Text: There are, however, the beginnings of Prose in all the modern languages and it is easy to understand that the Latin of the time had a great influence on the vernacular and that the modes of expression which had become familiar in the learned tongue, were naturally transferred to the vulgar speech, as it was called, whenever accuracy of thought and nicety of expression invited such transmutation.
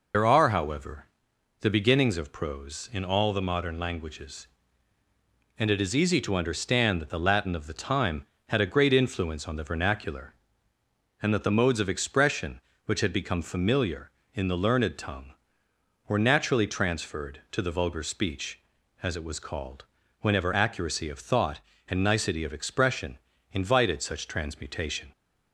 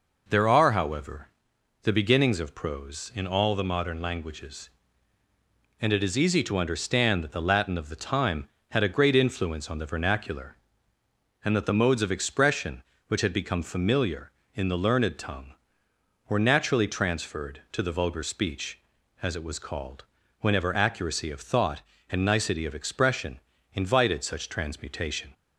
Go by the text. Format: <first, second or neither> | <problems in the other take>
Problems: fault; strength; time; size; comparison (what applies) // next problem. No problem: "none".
second | loses the start of "There"; at 0.1 s; 90 ms // pauses between "expression" and "invited"; slight; at 23.1 s; 0.34 s long; slight in the second